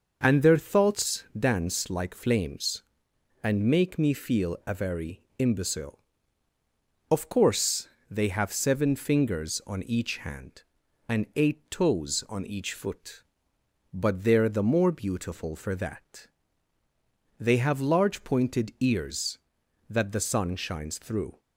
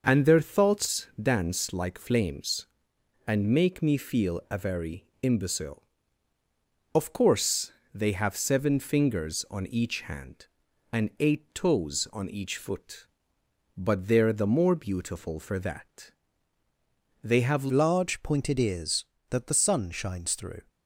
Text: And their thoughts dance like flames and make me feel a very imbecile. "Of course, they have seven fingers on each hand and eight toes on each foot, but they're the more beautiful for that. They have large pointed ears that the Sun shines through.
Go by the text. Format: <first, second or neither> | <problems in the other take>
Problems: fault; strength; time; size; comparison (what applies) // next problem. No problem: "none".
first | starts louder than the rest; noticeable; until 1.0 s; 6 dB; noticeable in the first // pauses between "very" and "imbecile"; slight; at 5.0 s; 0.16 s long; slight in the first // changes voice at "large"; from 17.7 s on; 2.9 s long